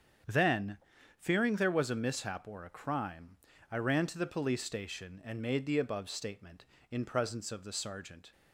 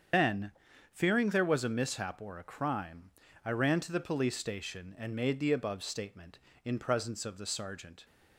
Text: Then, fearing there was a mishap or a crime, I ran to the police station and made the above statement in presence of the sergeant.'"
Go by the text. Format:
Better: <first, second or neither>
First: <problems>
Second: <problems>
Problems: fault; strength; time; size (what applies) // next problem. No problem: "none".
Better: first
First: starts louder than the rest; strong; until 1.6 s; 7.5 dB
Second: loses the start of "Then"; at 0.1 s; 155 ms // starts louder than the rest; strong; until 1.5 s; 7.5 dB